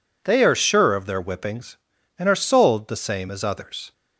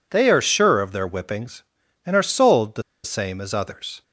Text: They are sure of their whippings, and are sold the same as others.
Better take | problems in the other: first | pauses between "the" and "same"; slight; at 2.8 s; 0.21 s long

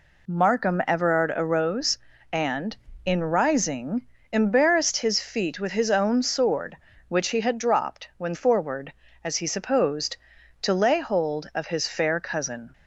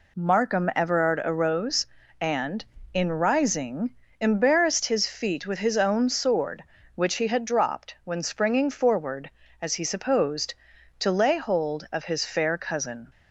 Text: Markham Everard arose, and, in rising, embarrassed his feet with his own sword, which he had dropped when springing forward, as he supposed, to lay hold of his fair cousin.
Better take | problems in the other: second | skips "springing"; at 8.3 s

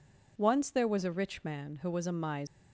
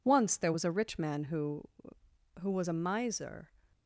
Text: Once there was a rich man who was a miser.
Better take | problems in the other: first | says "who" twice; at 2.4 s

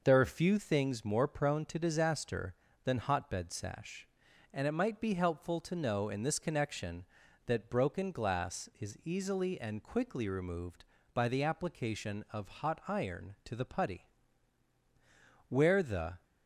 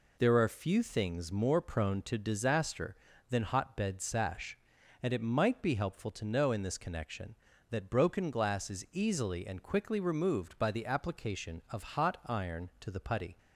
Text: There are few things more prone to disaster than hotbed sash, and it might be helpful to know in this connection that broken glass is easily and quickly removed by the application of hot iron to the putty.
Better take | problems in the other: second | goes on to say "Where the"; noticeable; from 15.4 s on; 0.74 s long

